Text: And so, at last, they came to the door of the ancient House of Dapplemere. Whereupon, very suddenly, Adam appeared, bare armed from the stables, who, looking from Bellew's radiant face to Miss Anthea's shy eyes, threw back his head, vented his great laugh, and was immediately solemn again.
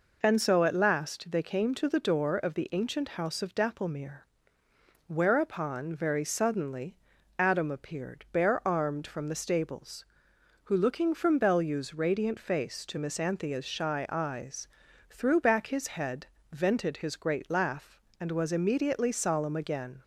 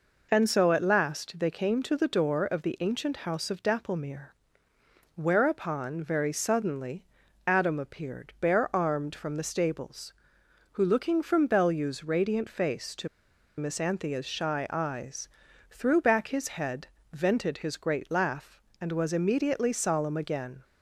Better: first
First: none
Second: pauses between "to" and "Miss"; noticeable; at 13.0 s; 0.50 s long

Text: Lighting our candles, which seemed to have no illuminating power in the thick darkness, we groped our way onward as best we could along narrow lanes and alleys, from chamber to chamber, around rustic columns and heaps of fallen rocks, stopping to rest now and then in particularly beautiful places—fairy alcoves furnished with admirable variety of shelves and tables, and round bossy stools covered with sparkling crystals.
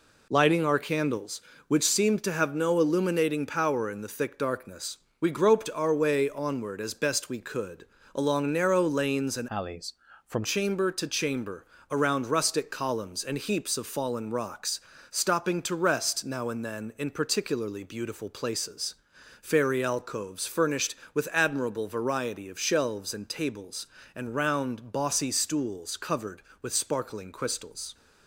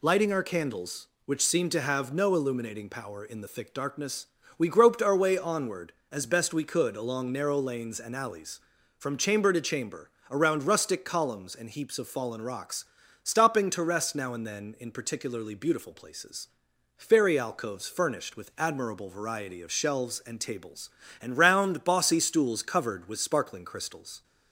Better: second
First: pauses between "could" and "along"; slight; at 7.8 s; 0.32 s long // changes voice from "alleys" to "from"; from 9.4 to 10.4 s; 1.0 s long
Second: none

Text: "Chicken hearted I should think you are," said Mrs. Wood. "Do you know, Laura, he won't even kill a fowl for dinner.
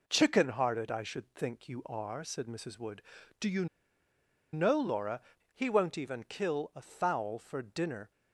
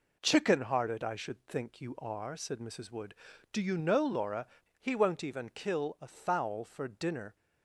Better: second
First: pauses between "you" and "know"; noticeable; at 3.6 s; 0.87 s long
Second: none

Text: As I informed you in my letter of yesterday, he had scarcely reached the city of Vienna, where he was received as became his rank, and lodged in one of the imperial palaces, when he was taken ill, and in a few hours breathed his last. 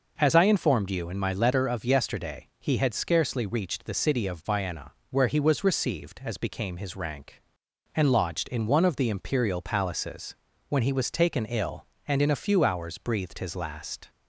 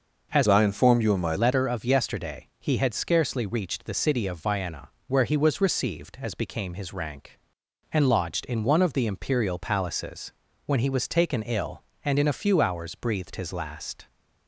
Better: first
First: none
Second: changes voice from "I" to "my"; from 0.4 to 1.3 s; 0.9 s long

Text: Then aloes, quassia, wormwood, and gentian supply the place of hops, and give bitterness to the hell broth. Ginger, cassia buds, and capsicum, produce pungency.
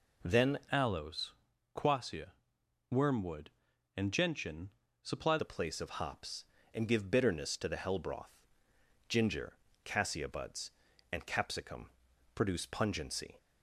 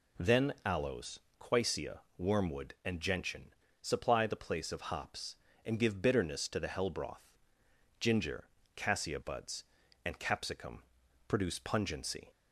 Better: second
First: changes voice from "aloes" to "supply"; from 0.7 to 5.3 s; 4.6 s long // pauses between "gentian" and "supply"; slight; at 4.7 s; 0.32 s long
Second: pauses between "gentian" and "supply"; slight; at 3.5 s; 0.30 s long

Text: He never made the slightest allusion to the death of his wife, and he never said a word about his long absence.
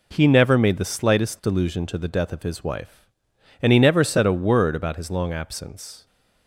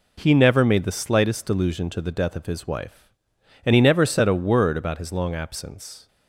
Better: neither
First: none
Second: none

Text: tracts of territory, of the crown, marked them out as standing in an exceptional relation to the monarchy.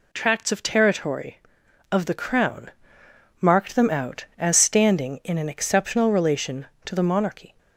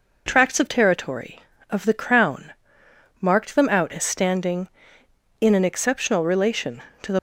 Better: first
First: none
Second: stops before "monarchy"; at 7.1 s

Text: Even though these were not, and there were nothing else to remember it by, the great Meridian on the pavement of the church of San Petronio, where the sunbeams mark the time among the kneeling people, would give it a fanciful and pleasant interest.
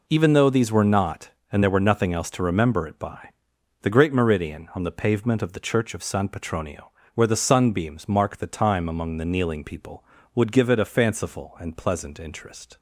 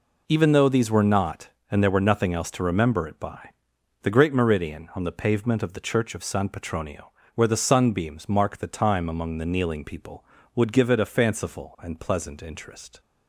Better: neither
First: none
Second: none

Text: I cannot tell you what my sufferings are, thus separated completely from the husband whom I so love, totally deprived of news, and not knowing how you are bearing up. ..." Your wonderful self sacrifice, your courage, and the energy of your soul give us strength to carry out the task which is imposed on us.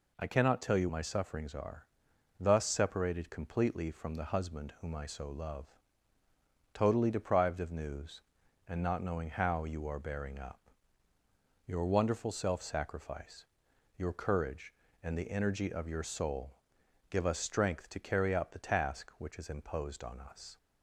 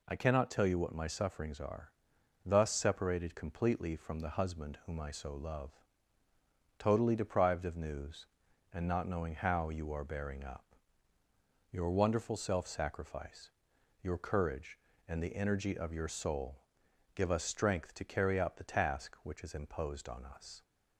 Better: second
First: skips "what"; at 0.8 s // pauses between "soul" and "give"; noticeable; at 16.5 s; 0.52 s long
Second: pauses between "soul" and "give"; noticeable; at 16.6 s; 0.52 s long

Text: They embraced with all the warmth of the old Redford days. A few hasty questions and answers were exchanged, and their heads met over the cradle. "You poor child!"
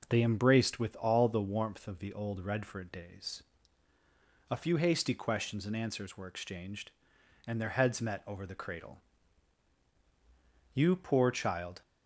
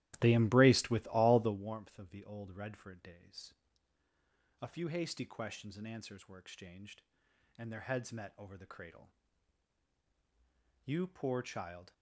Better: first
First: none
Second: starts louder than the rest; strong; until 1.6 s; 14.5 dB

